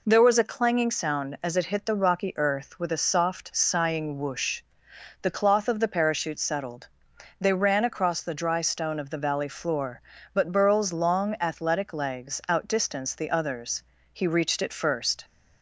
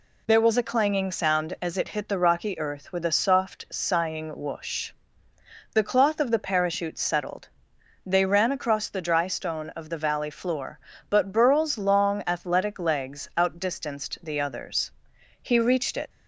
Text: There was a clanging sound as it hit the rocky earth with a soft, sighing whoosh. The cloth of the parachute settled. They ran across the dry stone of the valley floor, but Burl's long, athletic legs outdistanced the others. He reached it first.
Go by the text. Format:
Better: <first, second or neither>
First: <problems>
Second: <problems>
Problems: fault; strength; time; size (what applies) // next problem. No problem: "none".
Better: first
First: none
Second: stops before "first"; at 16.0 s